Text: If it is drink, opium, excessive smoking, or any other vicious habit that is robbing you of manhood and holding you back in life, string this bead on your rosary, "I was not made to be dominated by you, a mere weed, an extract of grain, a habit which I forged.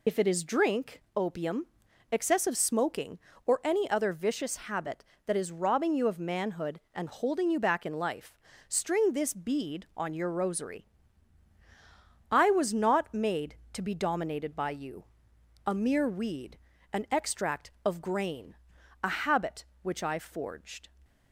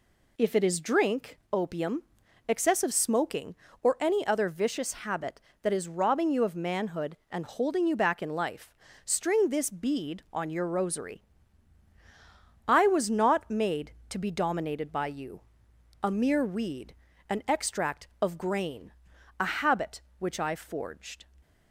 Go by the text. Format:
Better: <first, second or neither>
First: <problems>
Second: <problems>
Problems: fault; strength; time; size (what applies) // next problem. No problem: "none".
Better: second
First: loses the start of "If"; at 0.0 s; 55 ms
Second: none